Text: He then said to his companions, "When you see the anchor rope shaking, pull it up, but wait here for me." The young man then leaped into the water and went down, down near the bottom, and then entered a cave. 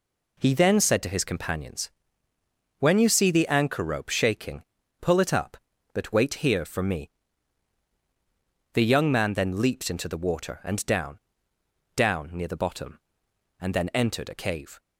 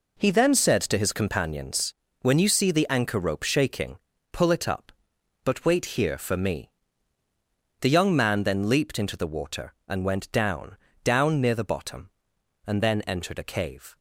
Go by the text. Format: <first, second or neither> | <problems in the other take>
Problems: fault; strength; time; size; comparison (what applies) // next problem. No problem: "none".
second | skips "went"; at 10.8 s